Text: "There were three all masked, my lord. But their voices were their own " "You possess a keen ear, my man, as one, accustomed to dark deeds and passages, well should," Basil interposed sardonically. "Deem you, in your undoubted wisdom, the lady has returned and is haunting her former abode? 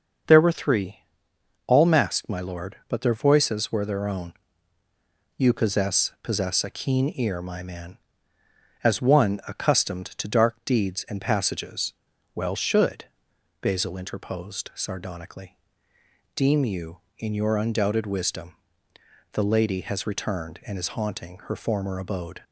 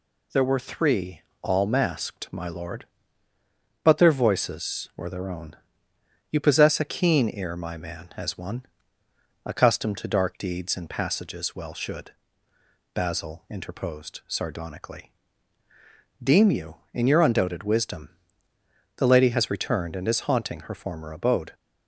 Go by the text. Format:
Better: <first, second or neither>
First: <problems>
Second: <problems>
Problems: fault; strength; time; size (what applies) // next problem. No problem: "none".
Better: second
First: starts louder than the rest; until 1.9 s; 6.5 dB // pauses between "three" and "all"; noticeable; at 0.9 s; 0.66 s long // says "possess" twice; at 6.2 s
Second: pauses between "three" and "all"; slight; at 1.2 s; 0.20 s long